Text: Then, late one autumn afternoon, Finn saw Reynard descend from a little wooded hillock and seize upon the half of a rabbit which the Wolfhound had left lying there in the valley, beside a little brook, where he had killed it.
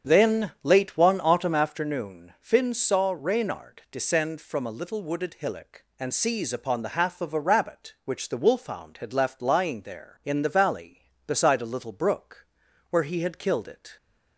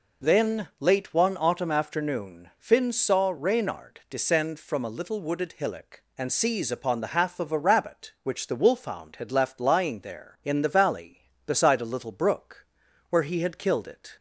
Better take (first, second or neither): second